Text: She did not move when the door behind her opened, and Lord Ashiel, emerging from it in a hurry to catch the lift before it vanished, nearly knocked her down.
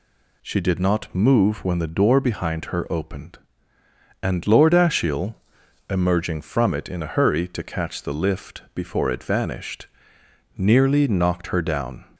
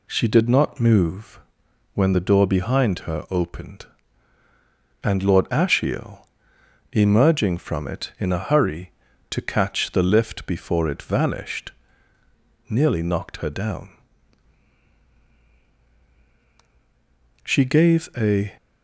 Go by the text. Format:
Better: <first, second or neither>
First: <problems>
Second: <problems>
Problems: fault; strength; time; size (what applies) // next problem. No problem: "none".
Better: first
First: none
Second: pauses between "move" and "when"; noticeable; at 1.3 s; 0.54 s long // goes on to say "She gave a"; noticeable; from 17.4 s on; 1.1 s long